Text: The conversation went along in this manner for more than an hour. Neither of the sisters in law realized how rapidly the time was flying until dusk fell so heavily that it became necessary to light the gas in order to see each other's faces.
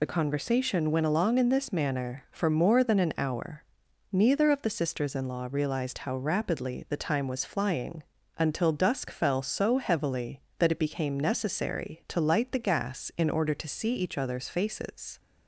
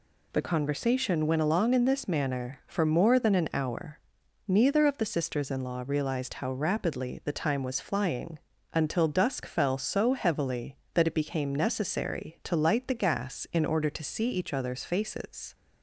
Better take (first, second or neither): second